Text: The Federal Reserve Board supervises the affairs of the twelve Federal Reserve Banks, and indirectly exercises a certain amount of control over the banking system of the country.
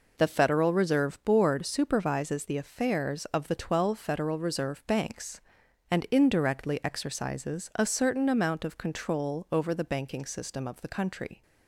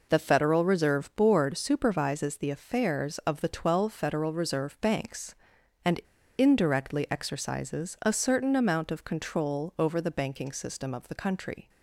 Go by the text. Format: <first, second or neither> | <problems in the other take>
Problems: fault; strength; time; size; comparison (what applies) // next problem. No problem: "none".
first | pauses between "and" and "indirectly"; at 5.9 s; 0.38 s long